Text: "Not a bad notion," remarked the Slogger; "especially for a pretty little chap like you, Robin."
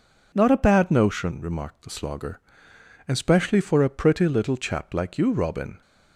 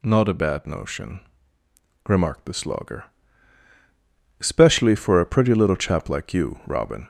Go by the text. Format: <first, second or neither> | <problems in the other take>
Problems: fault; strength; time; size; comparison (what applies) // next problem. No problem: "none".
first | gets louder; slight; throughout; 2 dB